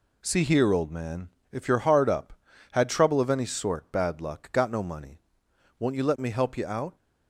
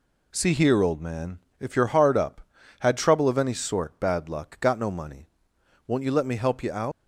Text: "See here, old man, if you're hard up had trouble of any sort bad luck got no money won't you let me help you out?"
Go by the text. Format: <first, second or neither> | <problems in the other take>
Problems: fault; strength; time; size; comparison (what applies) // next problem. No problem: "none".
first | pauses between "money" and "won't"; noticeable; at 5.2 s; 0.62 s long; noticeable in the first // leaves "out" unfinished; at 6.9 s; 90 ms